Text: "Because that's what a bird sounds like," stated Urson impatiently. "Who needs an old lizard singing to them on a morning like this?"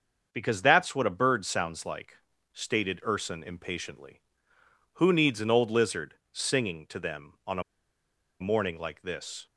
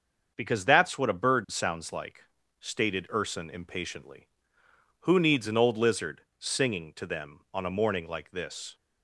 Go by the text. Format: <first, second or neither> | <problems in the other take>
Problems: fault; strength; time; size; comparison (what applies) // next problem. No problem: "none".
second | starts louder than the rest; until 1.3 s; 6.5 dB; also in the second // pauses between "lizard" and "singing"; slight; at 6.1 s; 0.16 s long; slight in the second // pauses between "a" and "morning"; noticeable; at 7.6 s; 0.79 s long